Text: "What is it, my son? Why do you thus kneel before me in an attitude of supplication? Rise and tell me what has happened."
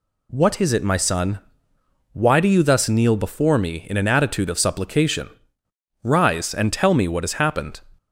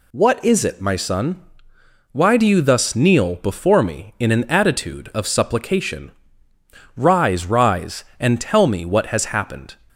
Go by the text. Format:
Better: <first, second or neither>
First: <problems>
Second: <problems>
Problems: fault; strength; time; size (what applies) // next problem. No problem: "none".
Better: first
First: none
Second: says "Rise" twice; at 7.4 s